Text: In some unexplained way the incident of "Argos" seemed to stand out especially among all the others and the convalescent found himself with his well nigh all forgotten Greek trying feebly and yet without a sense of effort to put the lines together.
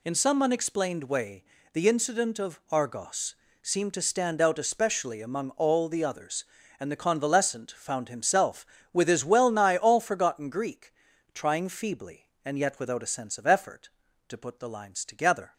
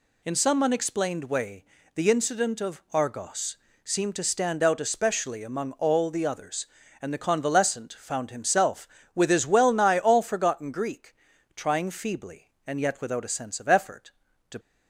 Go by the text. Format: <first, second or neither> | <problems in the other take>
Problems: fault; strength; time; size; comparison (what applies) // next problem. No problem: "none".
first | pauses between "way" and "the"; slight; at 1.6 s; 0.32 s long; slight in the first // pauses between "Argos" and "seemed"; slight; at 3.5 s; 0.28 s long; slight in the first // pauses between "Greek" and "trying"; at 11.1 s; 0.40 s long; also in the first // stops before "put the lines together"; at 14.5 s